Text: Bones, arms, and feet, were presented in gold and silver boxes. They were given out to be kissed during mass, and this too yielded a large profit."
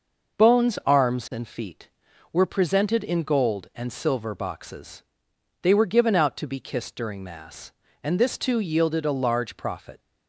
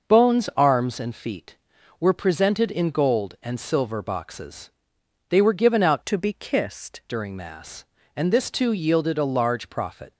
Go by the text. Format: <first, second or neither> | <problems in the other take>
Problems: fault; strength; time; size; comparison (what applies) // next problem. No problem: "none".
first | changes voice from "to" to "kissed"; from 6.0 to 7.0 s; 1.0 s long